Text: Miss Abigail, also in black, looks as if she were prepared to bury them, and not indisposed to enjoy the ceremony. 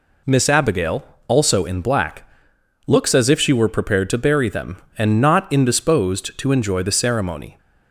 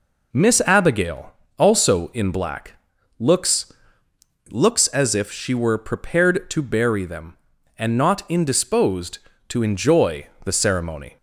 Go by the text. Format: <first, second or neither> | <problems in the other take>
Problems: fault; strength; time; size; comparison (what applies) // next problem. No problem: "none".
first | says "looks" twice; at 4.4 s // pauses between "enjoy" and "the"; slight; at 10.2 s; 0.18 s long